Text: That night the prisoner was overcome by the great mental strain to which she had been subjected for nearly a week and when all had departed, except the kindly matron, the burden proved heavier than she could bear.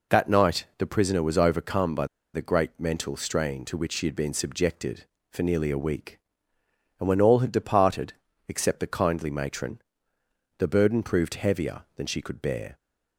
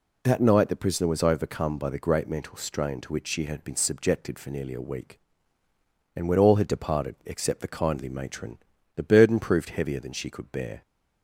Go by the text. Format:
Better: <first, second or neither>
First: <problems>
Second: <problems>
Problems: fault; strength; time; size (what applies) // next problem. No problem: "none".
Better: second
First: pauses between "by" and "the"; slight; at 2.0 s; 0.29 s long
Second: none